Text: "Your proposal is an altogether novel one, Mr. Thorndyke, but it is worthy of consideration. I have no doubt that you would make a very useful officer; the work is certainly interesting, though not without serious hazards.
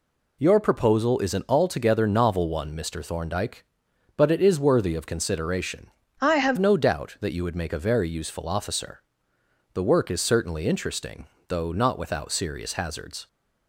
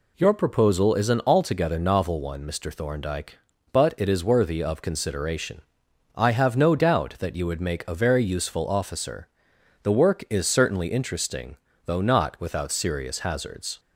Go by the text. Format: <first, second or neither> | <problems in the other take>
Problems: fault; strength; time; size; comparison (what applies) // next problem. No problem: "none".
second | changes voice from "I" to "have"; from 6.2 to 6.5 s; 0.3 s long